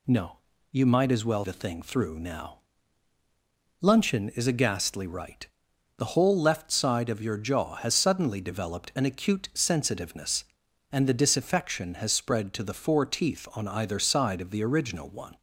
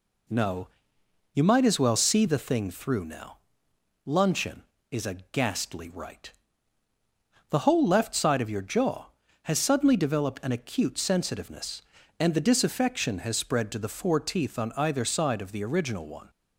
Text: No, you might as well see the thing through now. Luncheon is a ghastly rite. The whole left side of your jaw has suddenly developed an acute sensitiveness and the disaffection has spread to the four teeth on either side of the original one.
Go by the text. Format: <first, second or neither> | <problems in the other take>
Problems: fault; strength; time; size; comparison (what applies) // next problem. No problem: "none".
second | skips "see"; at 1.4 s